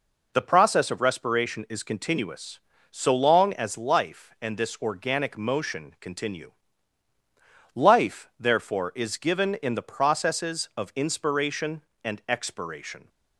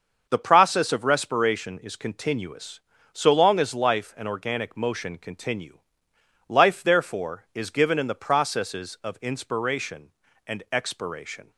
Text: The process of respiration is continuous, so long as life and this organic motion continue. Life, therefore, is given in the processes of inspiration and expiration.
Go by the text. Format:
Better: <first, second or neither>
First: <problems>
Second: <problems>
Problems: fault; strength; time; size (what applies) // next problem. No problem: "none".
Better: first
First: none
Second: starts louder than the rest; until 1.3 s; 6.5 dB // skips "this"; at 4.2 s